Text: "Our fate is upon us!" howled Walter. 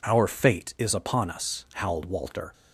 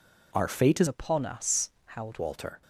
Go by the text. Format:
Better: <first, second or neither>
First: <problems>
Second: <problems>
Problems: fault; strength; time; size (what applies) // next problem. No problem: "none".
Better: first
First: none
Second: changes voice from "upon" to "howled"; from 0.8 to 2.1 s; 1.3 s long